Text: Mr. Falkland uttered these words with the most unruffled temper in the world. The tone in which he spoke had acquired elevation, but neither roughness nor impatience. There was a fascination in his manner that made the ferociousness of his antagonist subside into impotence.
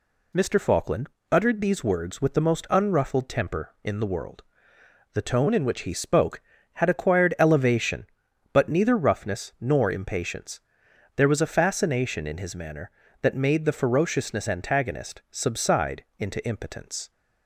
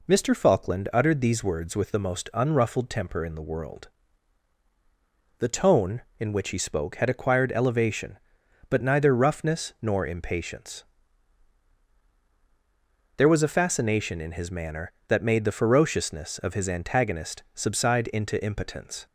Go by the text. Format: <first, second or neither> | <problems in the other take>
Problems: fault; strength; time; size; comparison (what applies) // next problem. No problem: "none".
second | pauses between "Falkland" and "uttered"; slight; at 1.0 s; 0.22 s long // skips "of his"; at 14.4 s // pauses between "subside" and "into"; slight; at 16.0 s; 0.16 s long